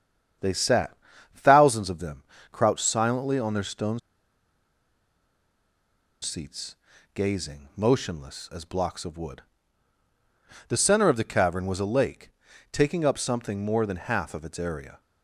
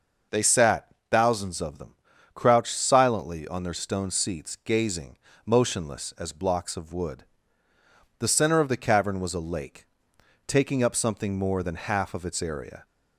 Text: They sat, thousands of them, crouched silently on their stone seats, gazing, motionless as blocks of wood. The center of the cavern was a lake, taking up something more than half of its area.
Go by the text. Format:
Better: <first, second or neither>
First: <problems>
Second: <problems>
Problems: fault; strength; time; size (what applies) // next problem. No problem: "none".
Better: second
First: starts louder than the rest; strong; until 1.8 s; 8.5 dB // pauses between "stone" and "seats"; strong; at 3.9 s; 2.2 s long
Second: none